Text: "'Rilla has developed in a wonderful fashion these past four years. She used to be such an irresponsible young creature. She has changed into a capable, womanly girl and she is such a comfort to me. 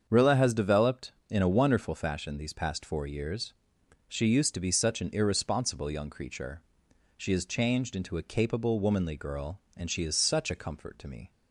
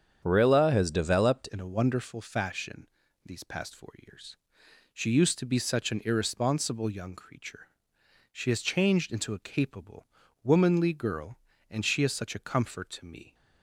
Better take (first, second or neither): first